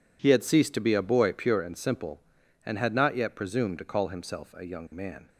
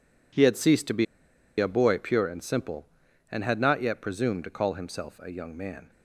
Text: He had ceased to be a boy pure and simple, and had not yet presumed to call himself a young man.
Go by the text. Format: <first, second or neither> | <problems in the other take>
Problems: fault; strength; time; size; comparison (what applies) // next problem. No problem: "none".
first | pauses between "be" and "a"; noticeable; at 1.0 s; 0.52 s long